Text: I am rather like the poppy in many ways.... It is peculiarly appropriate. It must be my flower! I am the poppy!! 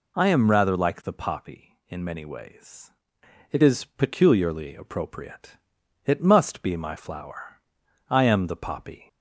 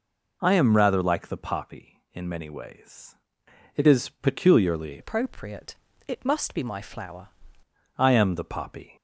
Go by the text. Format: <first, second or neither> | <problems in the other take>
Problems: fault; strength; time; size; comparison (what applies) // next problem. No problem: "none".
first | changes voice from "appropriate" to "flower"; from 4.9 to 7.2 s; 2.3 s long